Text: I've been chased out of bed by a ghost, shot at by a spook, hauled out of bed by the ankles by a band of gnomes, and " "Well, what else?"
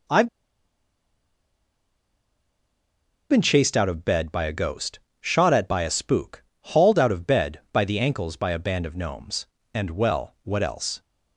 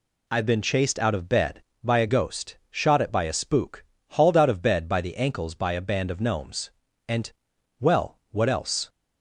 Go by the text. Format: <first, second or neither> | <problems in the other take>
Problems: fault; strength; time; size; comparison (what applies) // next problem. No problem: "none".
second | pauses between "I've" and "been"; strong; at 0.2 s; 3.0 s long